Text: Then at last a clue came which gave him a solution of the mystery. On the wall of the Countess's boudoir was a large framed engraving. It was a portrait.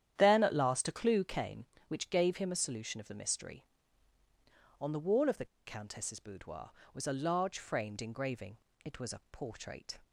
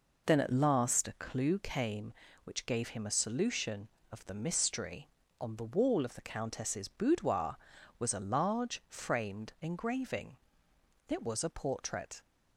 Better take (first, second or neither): second